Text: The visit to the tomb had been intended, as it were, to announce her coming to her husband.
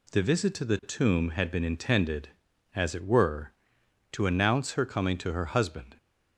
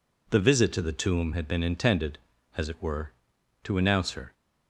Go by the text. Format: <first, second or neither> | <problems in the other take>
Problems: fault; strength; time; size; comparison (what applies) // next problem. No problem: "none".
first | stops before "coming to her husband"; at 4.3 s